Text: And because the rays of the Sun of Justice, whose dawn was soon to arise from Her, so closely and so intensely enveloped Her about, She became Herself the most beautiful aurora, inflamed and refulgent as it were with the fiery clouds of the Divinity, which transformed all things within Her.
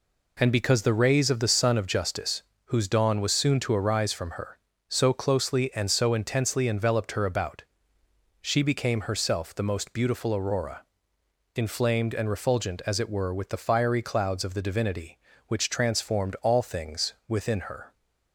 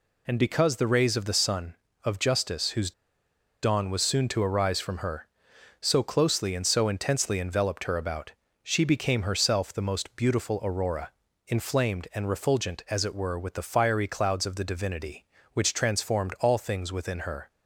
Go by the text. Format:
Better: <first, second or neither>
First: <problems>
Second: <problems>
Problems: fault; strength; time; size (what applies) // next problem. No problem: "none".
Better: first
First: none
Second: pauses between "whose" and "dawn"; noticeable; at 2.9 s; 0.71 s long